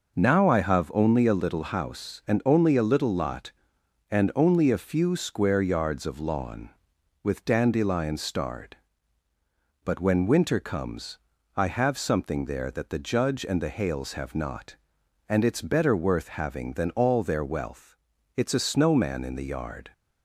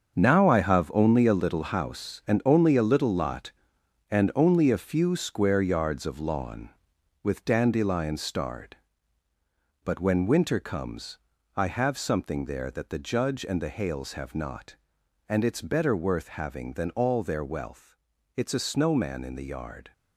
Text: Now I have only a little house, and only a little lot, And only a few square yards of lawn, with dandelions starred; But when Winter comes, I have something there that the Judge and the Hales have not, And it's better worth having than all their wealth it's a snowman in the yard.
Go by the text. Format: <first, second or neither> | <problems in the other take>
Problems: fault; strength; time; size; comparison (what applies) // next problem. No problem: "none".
first | gets quieter; strong; throughout; 10.5 dB // pauses between "wealth" and "it's"; at 17.9 s; 0.40 s long; also in the first